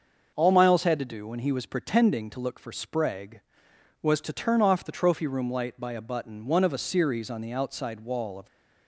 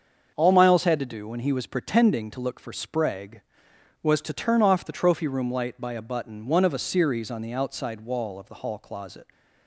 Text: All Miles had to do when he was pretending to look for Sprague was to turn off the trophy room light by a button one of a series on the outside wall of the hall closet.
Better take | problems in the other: second | starts louder than the rest; until 1.3 s; 6 dB; also in the second // stops before "the hall closet"; at 8.4 s

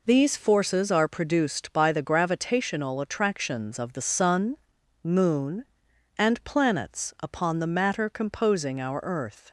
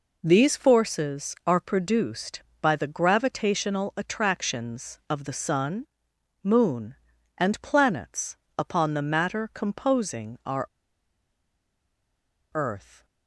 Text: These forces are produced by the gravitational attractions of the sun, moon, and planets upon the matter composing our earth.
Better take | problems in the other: first | pauses between "planets" and "upon"; slight; at 8.3 s; 0.18 s long // pauses between "our" and "earth"; strong; at 10.6 s; 1.8 s long

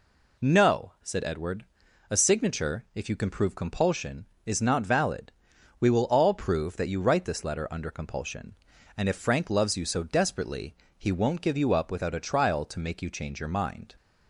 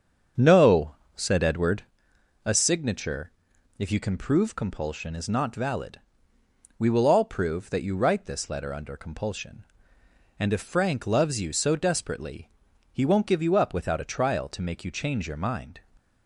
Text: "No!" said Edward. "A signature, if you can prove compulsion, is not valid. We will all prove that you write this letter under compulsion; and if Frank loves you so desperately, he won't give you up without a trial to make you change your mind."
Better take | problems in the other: first | starts louder than the rest; strong; until 1.9 s; 7 dB

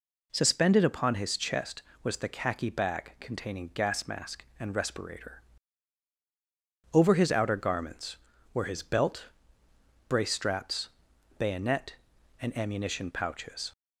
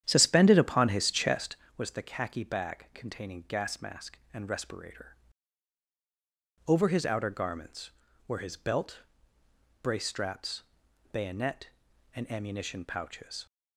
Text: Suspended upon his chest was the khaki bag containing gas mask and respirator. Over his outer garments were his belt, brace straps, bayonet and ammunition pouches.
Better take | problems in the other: first | starts louder than the rest; strong; until 1.7 s; 10 dB

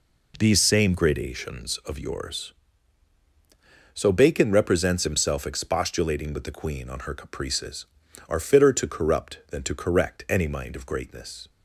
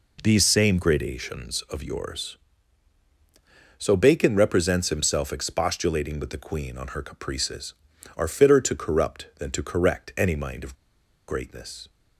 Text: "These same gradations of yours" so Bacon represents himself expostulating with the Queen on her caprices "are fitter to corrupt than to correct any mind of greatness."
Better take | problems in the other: first | pauses between "of" and "greatness"; noticeable; at 10.7 s; 0.54 s long

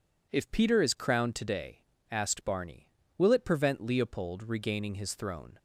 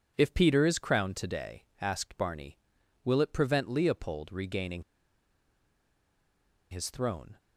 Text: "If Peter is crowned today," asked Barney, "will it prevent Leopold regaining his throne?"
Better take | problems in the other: first | pauses between "regaining" and "his"; strong; at 4.8 s; 1.8 s long

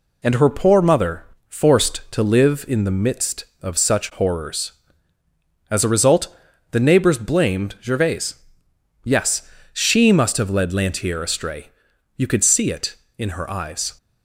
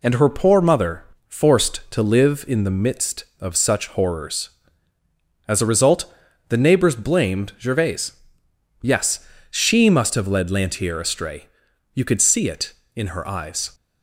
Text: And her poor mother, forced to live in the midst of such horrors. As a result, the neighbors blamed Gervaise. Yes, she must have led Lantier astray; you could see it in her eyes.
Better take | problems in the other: neither | none

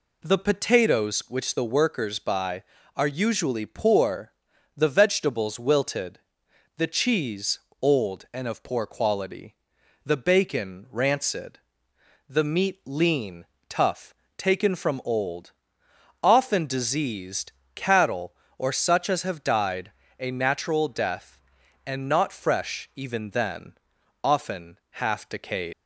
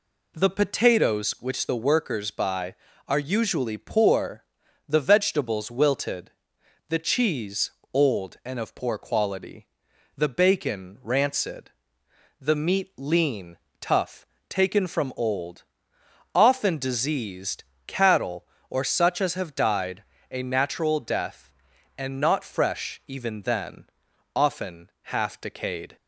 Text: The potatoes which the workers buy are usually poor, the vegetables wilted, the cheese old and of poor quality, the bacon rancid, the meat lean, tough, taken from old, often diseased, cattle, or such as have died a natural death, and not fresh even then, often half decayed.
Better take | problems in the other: second | pauses between "cheese" and "old"; slight; at 7.5 s; 0.24 s long; slight in the second // pauses between "died" and "a"; slight; at 19.9 s; 0.30 s long; slight in the second // leaves "decayed" unfinished; at 25.7 s; 110 ms

